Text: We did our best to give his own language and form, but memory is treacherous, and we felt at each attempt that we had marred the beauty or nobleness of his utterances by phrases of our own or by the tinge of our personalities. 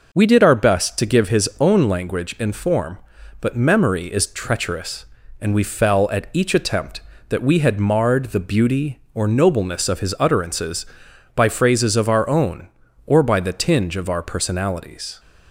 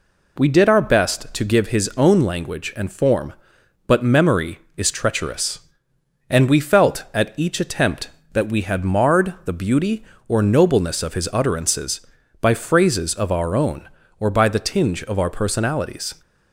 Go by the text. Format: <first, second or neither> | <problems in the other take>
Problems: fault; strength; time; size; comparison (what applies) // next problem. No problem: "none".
second | says "fell" for "felt"; at 5.6 s